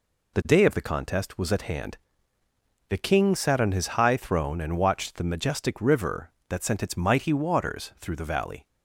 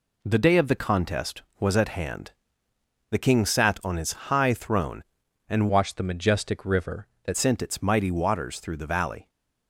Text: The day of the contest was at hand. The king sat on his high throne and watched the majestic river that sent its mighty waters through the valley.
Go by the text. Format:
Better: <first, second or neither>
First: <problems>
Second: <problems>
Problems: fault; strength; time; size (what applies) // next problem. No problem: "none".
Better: first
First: none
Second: changes voice from "watched" to "that"; from 5.6 to 7.3 s; 1.7 s long